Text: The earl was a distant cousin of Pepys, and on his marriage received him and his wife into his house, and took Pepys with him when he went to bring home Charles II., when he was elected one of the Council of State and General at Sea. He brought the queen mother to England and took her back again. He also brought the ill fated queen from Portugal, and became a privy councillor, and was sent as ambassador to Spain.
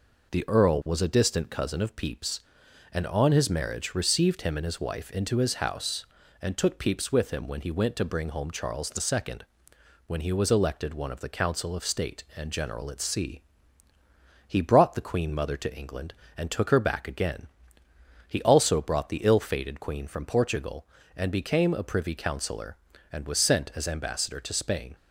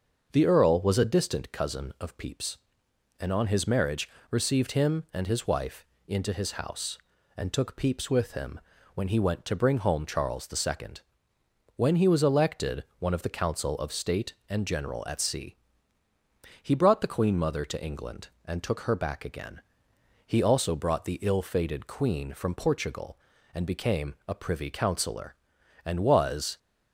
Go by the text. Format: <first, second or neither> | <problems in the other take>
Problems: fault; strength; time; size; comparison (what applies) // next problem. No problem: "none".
first | starts louder than the rest; until 1.3 s; 6.5 dB // pauses between "marriage" and "received"; slight; at 4.0 s; 0.22 s long // pauses between "wife" and "into"; slight; at 5.8 s; 0.22 s long // pauses between "him" and "when"; slight; at 8.6 s; 0.34 s long // stops before "sent as ambassador to Spain"; at 26.5 s